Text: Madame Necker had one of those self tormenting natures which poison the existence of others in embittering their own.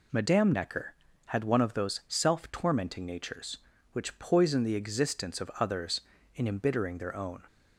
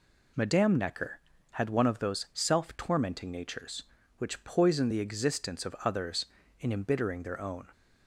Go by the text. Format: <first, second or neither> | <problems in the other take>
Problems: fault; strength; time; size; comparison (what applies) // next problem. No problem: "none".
neither | none